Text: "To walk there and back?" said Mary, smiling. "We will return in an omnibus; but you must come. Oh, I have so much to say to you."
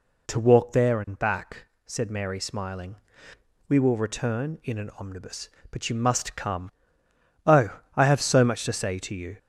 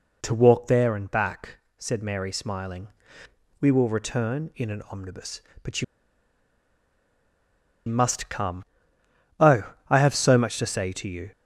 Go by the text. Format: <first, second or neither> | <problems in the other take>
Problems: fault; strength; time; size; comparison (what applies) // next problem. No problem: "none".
first | pauses between "you" and "must"; strong; at 5.8 s; 2.0 s long